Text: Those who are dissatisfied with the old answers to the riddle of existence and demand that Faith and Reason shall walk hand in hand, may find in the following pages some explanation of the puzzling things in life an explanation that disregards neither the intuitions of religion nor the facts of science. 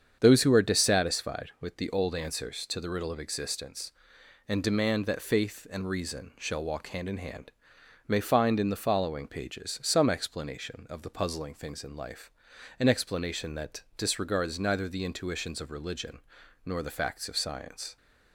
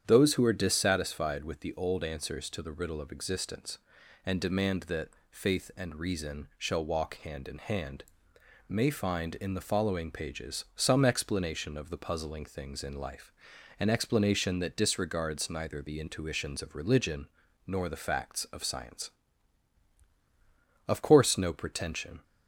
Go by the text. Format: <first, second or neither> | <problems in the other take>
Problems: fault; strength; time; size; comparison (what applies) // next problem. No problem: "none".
first | starts louder than the rest; strong; until 1.0 s; 9 dB; strong in the first // pauses between "that" and "Faith"; slight; at 5.0 s; 0.22 s long // pauses between "life" and "an"; noticeable; at 13.3 s; 0.48 s long; noticeable in the first // pauses between "religion" and "nor"; at 17.2 s; 0.40 s long; also in the first // goes on to say "Of course no pretension"; from 20.8 s on; 1.3 s long